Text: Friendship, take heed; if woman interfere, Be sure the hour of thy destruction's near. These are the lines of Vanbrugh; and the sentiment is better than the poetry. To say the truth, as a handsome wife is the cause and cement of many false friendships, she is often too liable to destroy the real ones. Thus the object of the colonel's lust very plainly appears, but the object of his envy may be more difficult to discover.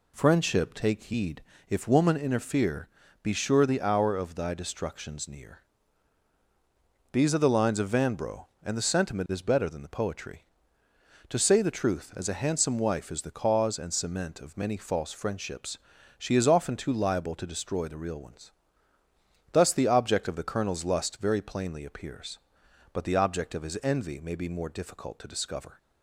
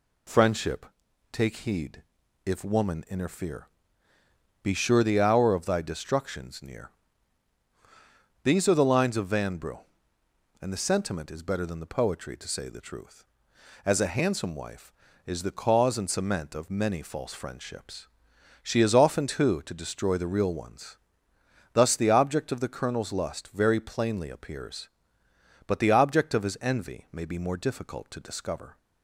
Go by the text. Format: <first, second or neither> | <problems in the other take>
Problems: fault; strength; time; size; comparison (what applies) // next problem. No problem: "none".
first | skips "liable"; at 19.6 s